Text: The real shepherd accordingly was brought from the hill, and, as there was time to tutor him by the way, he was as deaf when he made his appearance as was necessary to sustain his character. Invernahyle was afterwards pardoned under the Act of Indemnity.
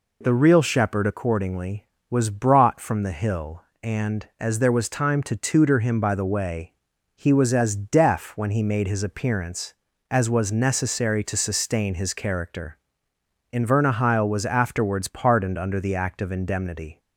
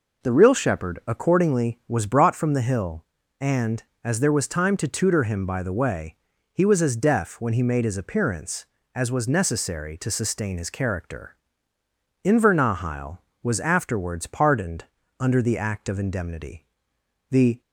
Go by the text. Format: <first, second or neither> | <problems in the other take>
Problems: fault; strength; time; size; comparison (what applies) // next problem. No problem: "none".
first | pauses between "pardoned" and "under"; slight; at 14.8 s; 0.36 s long // goes on to say "The"; slight; from 17.3 s on; 0.30 s long